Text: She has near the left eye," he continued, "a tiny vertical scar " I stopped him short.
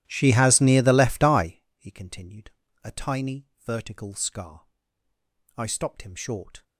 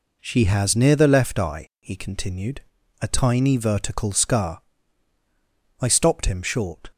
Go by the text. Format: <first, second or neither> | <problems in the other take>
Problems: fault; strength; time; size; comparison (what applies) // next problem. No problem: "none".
second | starts louder than the rest; strong; until 1.6 s; 14 dB // pauses between "tiny" and "vertical"; slight; at 3.4 s; 0.16 s long